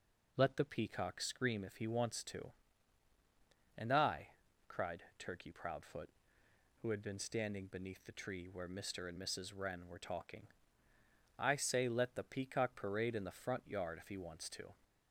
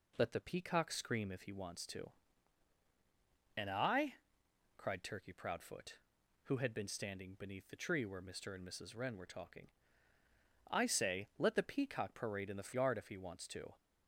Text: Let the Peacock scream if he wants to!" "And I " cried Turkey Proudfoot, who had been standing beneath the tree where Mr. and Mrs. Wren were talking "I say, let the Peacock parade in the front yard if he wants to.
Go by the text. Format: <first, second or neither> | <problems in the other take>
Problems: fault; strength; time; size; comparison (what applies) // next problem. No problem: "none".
first | pauses between "talking" and "I"; noticeable; at 9.7 s; 0.98 s long; noticeable in the first // skips "front"; at 12.7 s